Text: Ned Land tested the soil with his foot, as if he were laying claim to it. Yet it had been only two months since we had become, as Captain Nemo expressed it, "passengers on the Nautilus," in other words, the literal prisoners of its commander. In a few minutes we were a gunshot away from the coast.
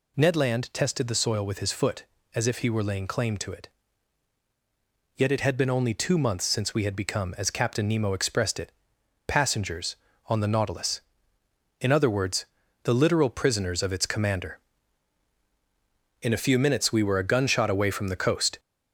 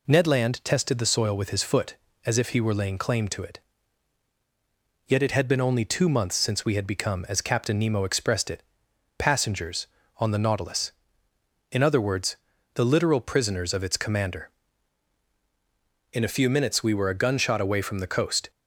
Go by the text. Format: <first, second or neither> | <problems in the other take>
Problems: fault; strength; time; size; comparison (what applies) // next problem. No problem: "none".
second | gets louder; throughout; 3.5 dB